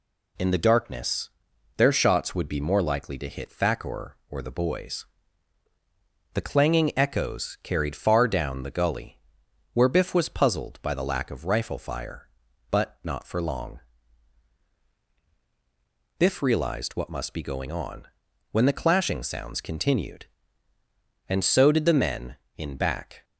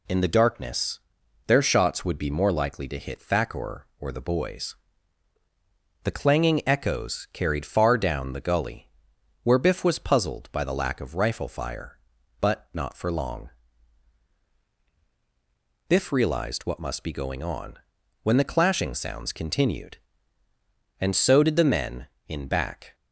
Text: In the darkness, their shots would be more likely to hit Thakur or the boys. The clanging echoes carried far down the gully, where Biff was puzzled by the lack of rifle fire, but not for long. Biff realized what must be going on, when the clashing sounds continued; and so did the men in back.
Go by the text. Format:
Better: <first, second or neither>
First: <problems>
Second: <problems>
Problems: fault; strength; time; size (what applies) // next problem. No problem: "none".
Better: neither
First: none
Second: none